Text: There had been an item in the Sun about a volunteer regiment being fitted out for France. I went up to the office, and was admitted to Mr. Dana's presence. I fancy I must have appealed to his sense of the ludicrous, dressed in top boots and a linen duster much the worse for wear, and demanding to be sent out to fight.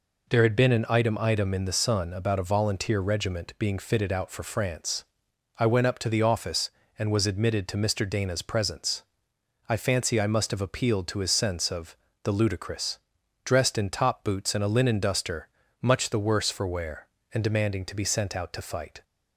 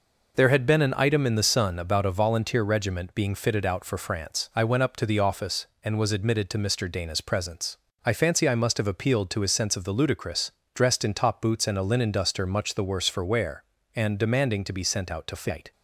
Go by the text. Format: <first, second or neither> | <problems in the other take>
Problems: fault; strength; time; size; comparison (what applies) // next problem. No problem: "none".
second | says "item" twice; at 1.1 s // pauses between "of" and "the"; slight; at 11.9 s; 0.28 s long // pauses between "duster" and "much"; slight; at 15.4 s; 0.34 s long